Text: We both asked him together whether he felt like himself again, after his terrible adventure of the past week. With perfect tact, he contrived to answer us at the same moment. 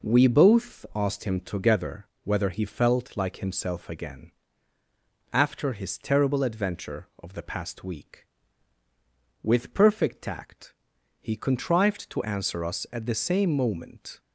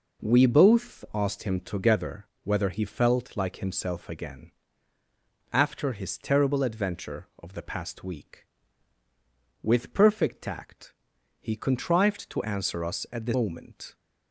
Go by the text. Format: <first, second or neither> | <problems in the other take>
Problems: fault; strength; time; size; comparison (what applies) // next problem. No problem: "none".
first | pauses between "together" and "whether"; slight; at 2.2 s; 0.18 s long; slight in the first // skips "same"; at 13.3 s